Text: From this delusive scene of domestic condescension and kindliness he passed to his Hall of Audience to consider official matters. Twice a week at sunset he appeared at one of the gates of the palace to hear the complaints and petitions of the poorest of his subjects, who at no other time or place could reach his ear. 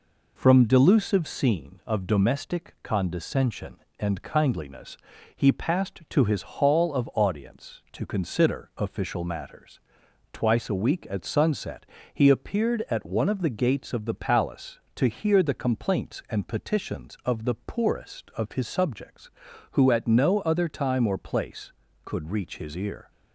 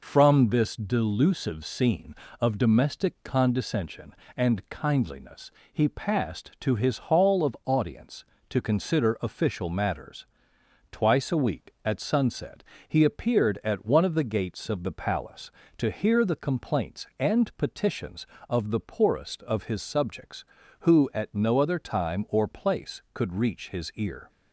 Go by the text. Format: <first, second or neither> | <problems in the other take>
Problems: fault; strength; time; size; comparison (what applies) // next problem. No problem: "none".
second | skips "this"; at 0.6 s // pauses between "kindliness" and "he"; slight; at 4.9 s; 0.36 s long; slight in the second // pauses between "sunset" and "he"; slight; at 11.8 s; 0.26 s long; slight in the second